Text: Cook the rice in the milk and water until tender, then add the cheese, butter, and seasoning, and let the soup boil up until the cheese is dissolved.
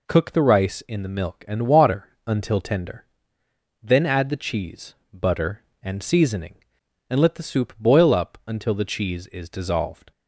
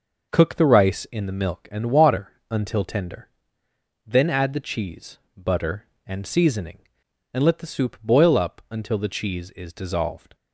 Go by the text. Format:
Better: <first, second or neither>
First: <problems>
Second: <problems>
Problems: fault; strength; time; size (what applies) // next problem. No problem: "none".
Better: first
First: pauses between "water" and "until"; slight; at 2.0 s; 0.18 s long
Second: starts louder than the rest; noticeable; until 1.7 s; 5.5 dB // pauses between "water" and "until"; slight; at 2.3 s; 0.18 s long